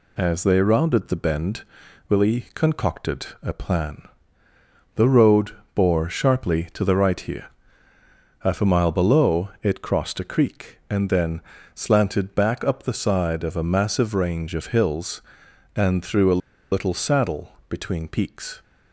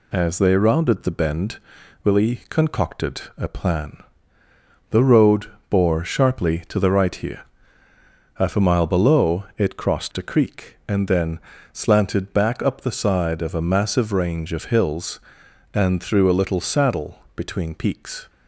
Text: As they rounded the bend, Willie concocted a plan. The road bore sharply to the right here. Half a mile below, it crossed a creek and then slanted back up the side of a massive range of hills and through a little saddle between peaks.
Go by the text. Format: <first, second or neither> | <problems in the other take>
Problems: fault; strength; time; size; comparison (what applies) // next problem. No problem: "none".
second | pauses between "concocted" and "a"; slight; at 3.2 s; 0.16 s long; slight in the second // pauses between "road" and "bore"; slight; at 5.5 s; 0.24 s long; slight in the second // pauses between "then" and "slanted"; slight; at 11.4 s; 0.34 s long; slight in the second // pauses between "a" and "little"; slight; at 16.4 s; 0.32 s long // pauses between "saddle" and "between"; slight; at 17.5 s; 0.16 s long; slight in the second